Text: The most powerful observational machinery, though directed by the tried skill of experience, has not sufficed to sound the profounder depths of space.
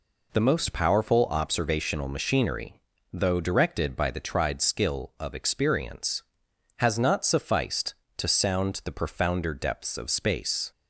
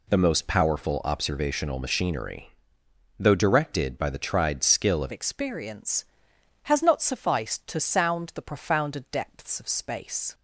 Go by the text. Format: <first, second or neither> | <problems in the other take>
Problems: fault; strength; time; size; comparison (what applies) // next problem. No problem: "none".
first | changes voice at "experience"; from 5.1 s on; 5.2 s long